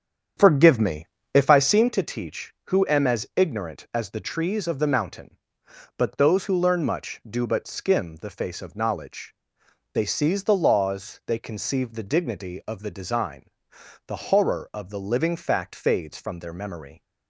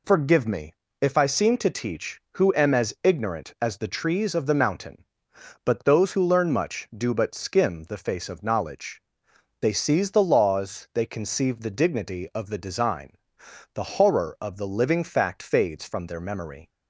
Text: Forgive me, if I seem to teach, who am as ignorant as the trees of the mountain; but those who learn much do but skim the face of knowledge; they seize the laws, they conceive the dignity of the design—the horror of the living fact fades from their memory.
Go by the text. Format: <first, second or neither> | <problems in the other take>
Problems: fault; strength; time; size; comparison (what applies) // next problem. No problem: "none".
second | starts louder than the rest; strong; until 2.0 s; 8.5 dB